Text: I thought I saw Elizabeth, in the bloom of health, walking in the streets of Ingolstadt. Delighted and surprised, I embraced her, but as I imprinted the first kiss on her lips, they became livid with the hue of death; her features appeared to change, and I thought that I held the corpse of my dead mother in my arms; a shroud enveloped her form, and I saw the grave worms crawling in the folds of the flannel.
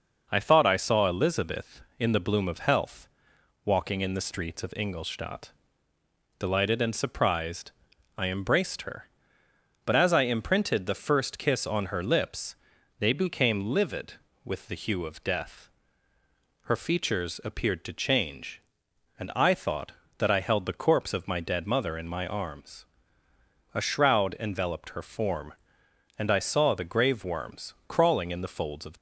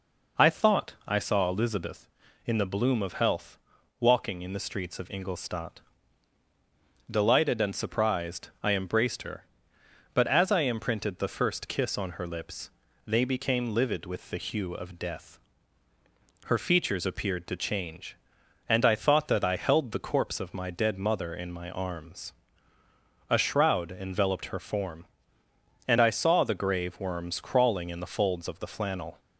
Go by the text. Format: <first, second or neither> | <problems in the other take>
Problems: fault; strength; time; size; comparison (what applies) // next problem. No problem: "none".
second | stops before "the flannel"; at 28.9 s